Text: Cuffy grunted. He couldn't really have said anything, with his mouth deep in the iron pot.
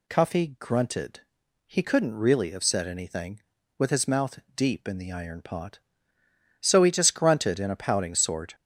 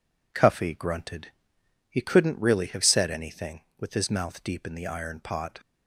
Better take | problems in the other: second | pauses between "mouth" and "deep"; slight; at 4.3 s; 0.16 s long // goes on to say "So he just grunted in a pouting sort"; strong; from 6.6 s on; 1.9 s long

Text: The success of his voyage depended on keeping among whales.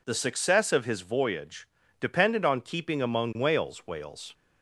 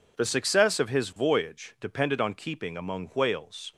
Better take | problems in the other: second | pauses between "voyage" and "depended"; slight; at 1.6 s; 0.32 s long // says "whales" twice; at 3.8 s

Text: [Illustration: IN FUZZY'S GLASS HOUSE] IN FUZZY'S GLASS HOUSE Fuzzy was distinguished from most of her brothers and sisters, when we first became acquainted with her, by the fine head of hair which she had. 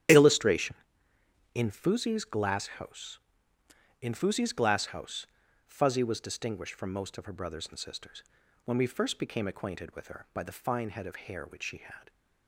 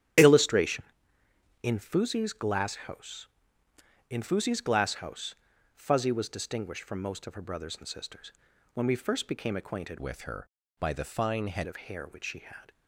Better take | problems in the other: first | starts louder than the rest; strong; until 1.9 s; 11 dB; strong in the first // pauses between "HOUSE" and "Fuzzy"; at 5.3 s; 0.44 s long; also in the first // changes voice from "with" to "head"; from 9.9 to 11.6 s; 1.7 s long

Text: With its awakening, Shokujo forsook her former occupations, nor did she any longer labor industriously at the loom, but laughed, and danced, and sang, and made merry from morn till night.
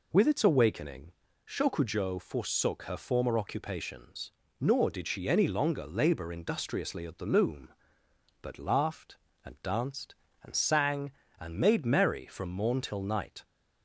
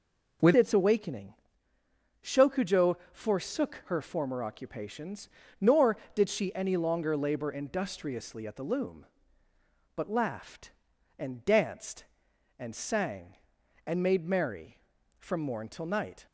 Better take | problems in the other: first | changes voice at "its"; from 0.5 s on; 15.7 s long // pauses between "Shokujo" and "forsook"; slight; at 2.9 s; 0.16 s long

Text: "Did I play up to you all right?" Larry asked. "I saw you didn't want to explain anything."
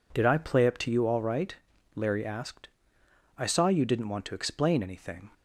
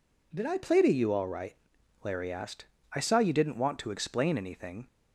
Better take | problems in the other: first | skips "up"; at 0.8 s

